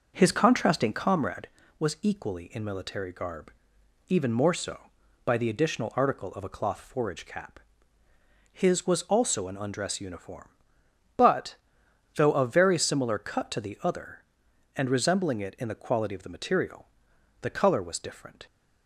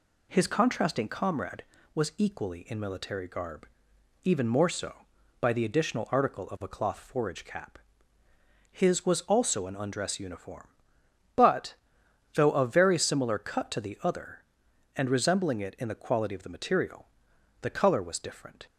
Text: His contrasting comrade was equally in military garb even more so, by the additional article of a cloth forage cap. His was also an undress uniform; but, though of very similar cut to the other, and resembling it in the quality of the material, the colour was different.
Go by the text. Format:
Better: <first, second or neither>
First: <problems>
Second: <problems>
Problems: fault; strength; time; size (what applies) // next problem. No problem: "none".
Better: second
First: starts louder than the rest; noticeable; until 1.4 s; 5 dB // pauses between "garb" and "even"; noticeable; at 3.5 s; 0.56 s long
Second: pauses between "garb" and "even"; noticeable; at 3.6 s; 0.56 s long